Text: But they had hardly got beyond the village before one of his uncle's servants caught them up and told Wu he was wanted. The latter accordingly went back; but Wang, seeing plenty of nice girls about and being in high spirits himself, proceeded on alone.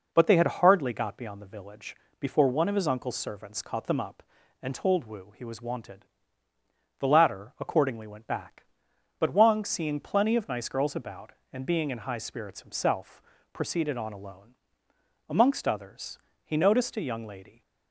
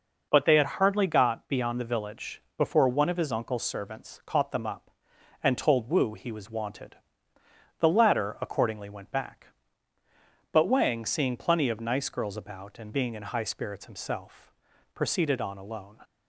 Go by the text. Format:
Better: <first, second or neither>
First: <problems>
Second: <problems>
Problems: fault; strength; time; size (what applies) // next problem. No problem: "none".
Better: second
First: pauses between "village" and "before"; slight; at 1.9 s; 0.24 s long // goes on to say "Amongst others he noticed a young lady"; strong; from 15.2 s on; 2.3 s long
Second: pauses between "village" and "before"; slight; at 2.4 s; 0.16 s long